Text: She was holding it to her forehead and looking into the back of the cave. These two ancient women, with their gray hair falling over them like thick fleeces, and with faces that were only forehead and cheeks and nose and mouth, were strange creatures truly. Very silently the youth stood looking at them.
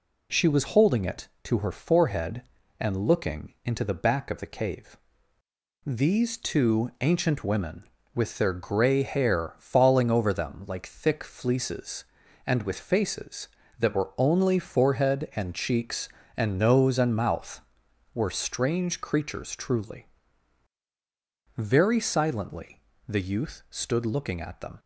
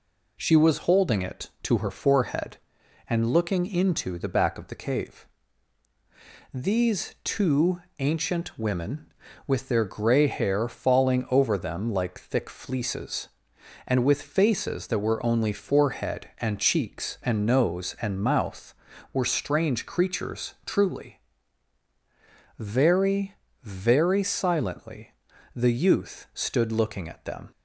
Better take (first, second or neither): first